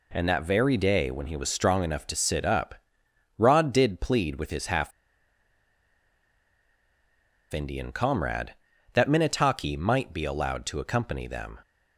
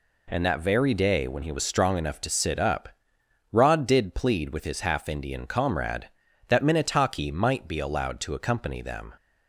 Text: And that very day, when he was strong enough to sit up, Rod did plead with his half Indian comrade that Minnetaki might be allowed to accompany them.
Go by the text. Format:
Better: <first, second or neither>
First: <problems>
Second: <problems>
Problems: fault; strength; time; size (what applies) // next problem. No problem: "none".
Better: second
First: pauses between "half" and "Indian"; strong; at 4.9 s; 2.6 s long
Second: none